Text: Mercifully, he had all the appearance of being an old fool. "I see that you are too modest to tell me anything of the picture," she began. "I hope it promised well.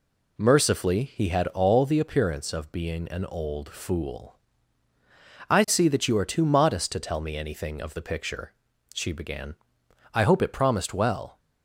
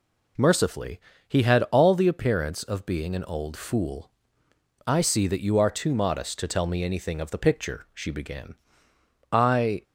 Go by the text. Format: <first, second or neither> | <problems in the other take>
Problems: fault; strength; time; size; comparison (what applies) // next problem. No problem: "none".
first | stops before "hope it promised well"; at 9.8 s